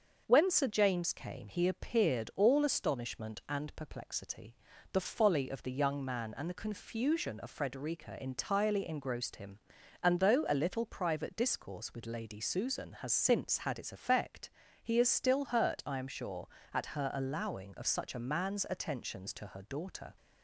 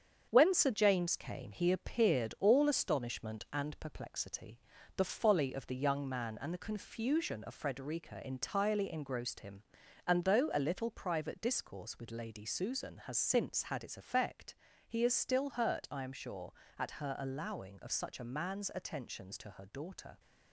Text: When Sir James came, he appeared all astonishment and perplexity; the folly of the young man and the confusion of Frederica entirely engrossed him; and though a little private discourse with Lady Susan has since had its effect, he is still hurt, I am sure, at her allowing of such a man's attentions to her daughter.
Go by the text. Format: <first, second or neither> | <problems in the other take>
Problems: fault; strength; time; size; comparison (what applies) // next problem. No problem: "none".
first | gets quieter; noticeable; throughout; 5.5 dB // starts louder than the rest; strong; until 1.3 s; 7.5 dB; also in the first